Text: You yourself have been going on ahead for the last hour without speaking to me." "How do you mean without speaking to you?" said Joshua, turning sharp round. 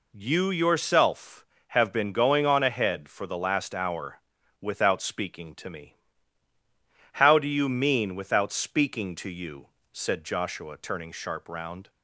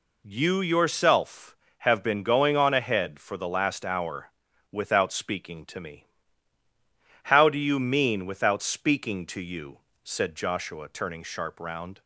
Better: neither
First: pauses between "hour" and "without"; at 4.1 s; 0.40 s long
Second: pauses between "hour" and "without"; at 4.2 s; 0.40 s long

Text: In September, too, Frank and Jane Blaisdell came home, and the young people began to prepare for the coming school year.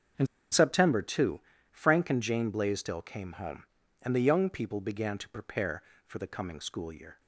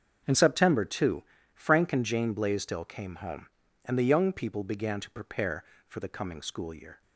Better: second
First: starts louder than the rest; until 1.4 s; 7 dB // pauses between "In" and "September"; slight; at 0.2 s; 0.25 s long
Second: starts louder than the rest; until 1.5 s; 7 dB

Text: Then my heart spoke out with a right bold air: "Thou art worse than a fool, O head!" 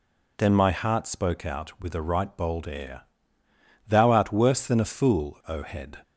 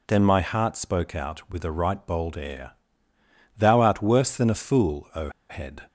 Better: first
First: none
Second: pauses between "O" and "head"; slight; at 5.2 s; 0.20 s long

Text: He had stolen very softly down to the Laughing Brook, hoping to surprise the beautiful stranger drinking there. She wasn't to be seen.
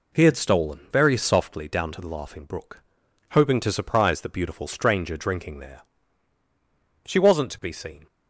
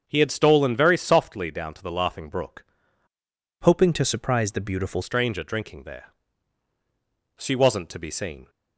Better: first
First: none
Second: starts louder than the rest; until 1.0 s; 7 dB // changes voice from "hoping" to "beautiful"; from 3.6 to 5.0 s; 1.4 s long

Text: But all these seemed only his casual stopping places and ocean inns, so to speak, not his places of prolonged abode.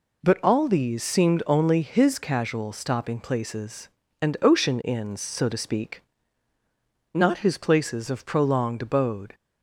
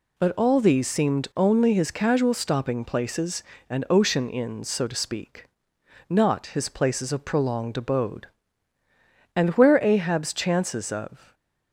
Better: first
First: none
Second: goes on to say "And where Ahab's chances of"; strong; from 9.3 s on; 2.0 s long // stays silent after the last word; slight; from 11.1 s on; 0.6 s long

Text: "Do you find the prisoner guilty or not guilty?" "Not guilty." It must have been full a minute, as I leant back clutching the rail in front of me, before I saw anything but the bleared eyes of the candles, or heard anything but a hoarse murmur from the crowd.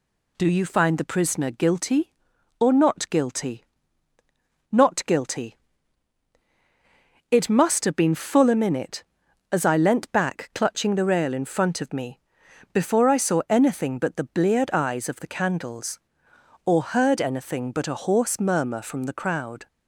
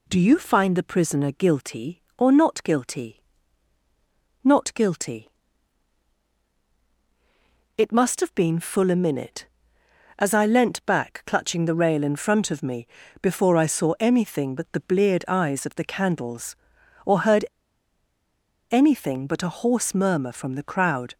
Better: first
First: none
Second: pauses between "heard" and "anything"; at 17.4 s; 1.2 s long

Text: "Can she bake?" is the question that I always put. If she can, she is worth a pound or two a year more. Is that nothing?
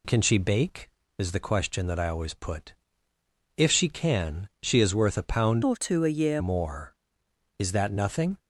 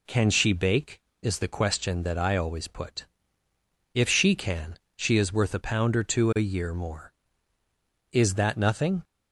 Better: second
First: changes voice from "or" to "year"; from 5.6 to 6.4 s; 0.8 s long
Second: none

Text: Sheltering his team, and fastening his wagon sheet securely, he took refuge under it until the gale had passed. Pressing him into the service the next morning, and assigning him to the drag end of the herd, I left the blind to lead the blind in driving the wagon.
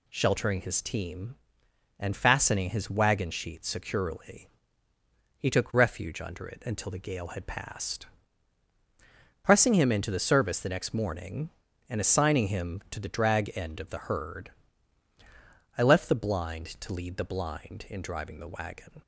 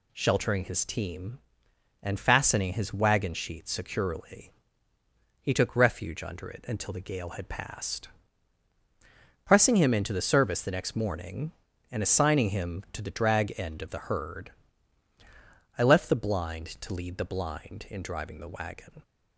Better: neither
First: none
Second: none

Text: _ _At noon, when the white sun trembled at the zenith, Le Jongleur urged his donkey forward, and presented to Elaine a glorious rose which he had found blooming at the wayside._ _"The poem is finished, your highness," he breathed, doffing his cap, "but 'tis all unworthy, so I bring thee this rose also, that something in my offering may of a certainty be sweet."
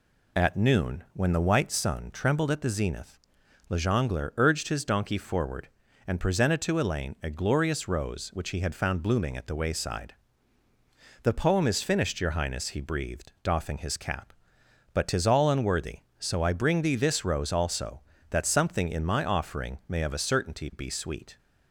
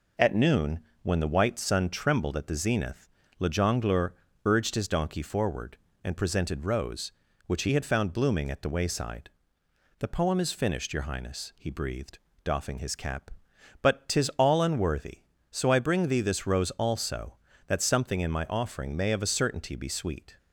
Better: first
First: none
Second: pauses between "Jongleur" and "urged"; slight; at 4.1 s; 0.32 s long // skips "to Elaine a glorious"; at 6.6 s

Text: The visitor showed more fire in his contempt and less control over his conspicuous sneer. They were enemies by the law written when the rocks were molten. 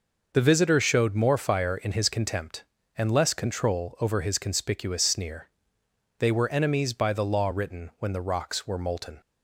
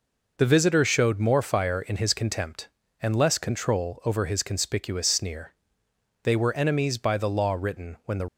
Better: first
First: none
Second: stops before "rocks were molten"; at 8.2 s

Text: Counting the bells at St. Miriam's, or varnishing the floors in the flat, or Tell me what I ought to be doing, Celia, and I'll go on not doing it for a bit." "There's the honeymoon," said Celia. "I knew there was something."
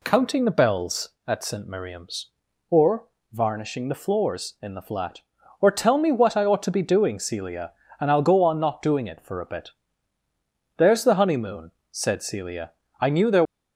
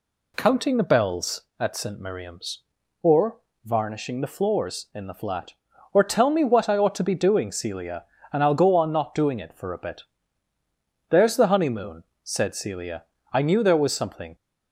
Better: second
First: pauses between "or" and "varnishing"; slight; at 3.0 s; 0.26 s long // stops before "was something"; at 13.4 s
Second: pauses between "or" and "varnishing"; slight; at 3.3 s; 0.26 s long

